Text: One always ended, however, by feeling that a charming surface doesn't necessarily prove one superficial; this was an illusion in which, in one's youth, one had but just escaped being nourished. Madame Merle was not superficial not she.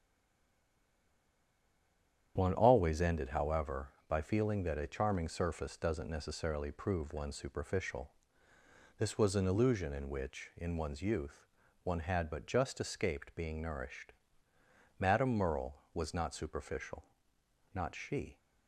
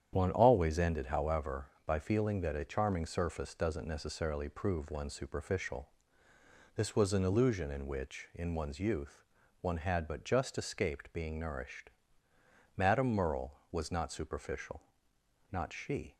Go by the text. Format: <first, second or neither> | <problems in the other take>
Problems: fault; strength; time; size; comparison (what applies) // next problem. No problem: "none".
second | stays silent before the first word; until 2.3 s; 2.3 s long // starts louder than the rest; strong; until 3.3 s; 9 dB; strong in the second // pauses between "superficial" and "not"; noticeable; at 17.0 s; 0.68 s long; noticeable in the second